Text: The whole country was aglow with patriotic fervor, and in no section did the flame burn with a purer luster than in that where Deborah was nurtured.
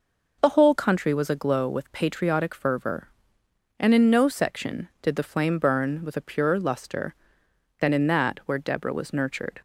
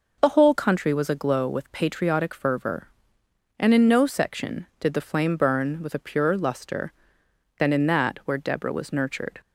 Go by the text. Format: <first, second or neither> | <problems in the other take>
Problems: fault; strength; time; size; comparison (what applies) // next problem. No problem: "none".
neither | none